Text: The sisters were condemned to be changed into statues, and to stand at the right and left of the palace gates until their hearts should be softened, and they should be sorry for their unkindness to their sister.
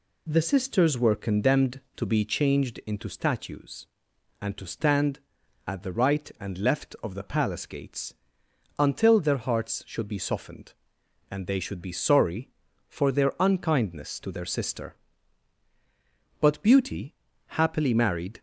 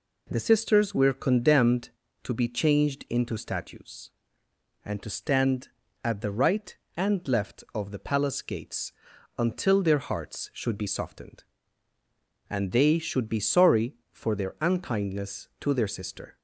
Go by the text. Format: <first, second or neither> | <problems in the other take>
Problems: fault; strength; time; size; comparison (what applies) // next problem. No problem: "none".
second | pauses between "gates" and "until"; noticeable; at 8.1 s; 0.64 s long; noticeable in the second // goes on to say "But Beauty happily married"; strong; from 16.4 s on; 2.0 s long